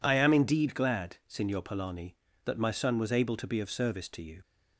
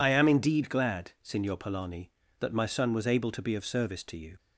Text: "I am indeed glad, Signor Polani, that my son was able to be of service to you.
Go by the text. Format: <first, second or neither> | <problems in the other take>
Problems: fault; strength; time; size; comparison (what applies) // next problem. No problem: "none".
first | loses the start of "I"; at 0.0 s; 40 ms